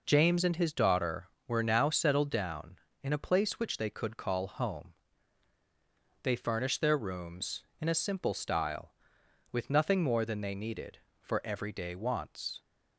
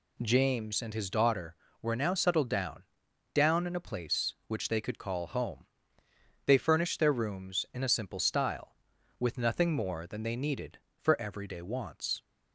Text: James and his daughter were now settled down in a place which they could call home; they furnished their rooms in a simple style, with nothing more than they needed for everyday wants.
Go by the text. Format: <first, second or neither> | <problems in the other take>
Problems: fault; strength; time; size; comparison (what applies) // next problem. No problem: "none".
first | says "down" twice; at 3.3 s